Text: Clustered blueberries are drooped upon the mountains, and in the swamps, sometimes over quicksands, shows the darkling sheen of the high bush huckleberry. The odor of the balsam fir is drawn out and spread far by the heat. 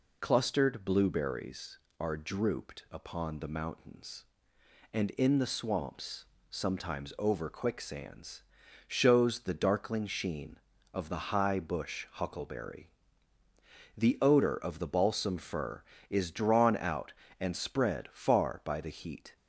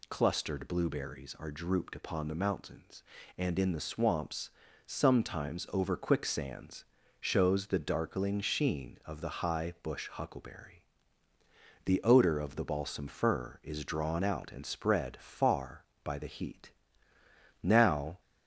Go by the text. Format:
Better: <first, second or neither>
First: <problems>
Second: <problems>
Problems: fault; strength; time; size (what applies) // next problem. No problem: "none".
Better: first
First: none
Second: goes on to say "Now"; from 17.5 s on; 0.60 s long